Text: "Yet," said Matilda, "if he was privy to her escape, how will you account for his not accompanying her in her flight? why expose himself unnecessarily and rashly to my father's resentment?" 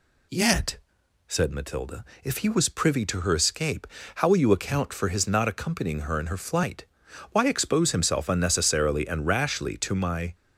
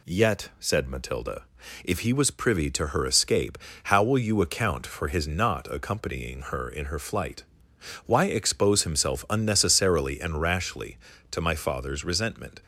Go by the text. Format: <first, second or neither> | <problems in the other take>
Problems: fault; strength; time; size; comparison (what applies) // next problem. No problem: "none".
second | stops before "father's resentment"; at 10.3 s